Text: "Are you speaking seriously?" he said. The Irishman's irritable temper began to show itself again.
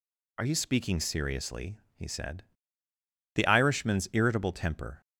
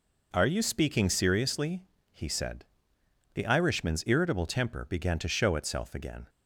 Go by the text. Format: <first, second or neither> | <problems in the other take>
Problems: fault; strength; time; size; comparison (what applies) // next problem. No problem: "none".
second | stops before "began to show itself again"; at 5.0 s